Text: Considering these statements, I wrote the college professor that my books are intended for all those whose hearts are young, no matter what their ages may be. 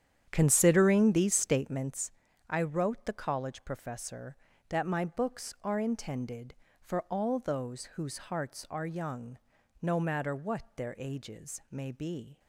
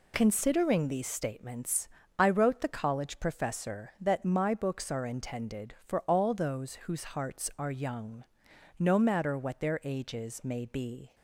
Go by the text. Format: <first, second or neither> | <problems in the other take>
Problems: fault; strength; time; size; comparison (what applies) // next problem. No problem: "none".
second | starts louder than the rest; strong; until 2.0 s; 9 dB